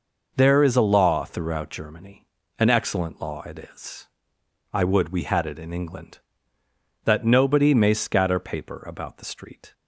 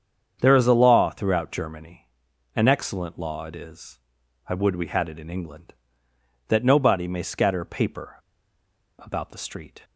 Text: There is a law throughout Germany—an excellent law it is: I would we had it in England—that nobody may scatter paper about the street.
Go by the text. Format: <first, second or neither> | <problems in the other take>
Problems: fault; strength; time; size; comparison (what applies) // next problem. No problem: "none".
first | starts louder than the rest; strong; until 1.4 s; 7.5 dB // pauses between "paper" and "about"; noticeable; at 8.1 s; 0.81 s long